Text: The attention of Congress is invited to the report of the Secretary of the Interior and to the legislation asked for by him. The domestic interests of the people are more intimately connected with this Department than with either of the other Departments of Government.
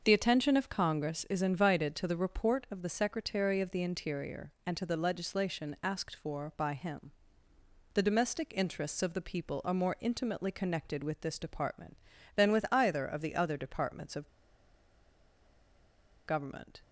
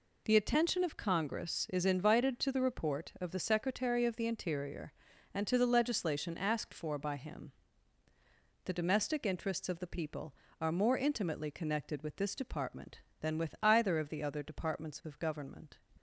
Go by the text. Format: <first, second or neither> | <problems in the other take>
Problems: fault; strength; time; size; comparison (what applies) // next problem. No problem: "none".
second | starts louder than the rest; until 1.0 s; 6.5 dB // pauses between "of" and "Government"; strong; at 14.2 s; 1.9 s long